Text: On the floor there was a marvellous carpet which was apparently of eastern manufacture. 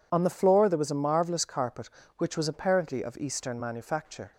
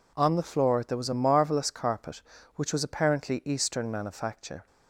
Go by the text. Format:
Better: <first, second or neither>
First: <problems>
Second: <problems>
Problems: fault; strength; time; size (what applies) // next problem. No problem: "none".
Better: first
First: none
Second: skips "of"; at 3.4 s